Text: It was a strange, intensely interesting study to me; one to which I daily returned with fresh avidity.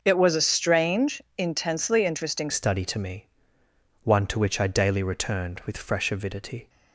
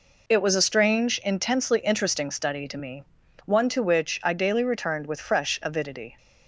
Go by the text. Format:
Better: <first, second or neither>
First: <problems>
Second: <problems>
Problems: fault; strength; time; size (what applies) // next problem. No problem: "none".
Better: second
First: changes voice at "study"; from 2.4 s on; 4.2 s long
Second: none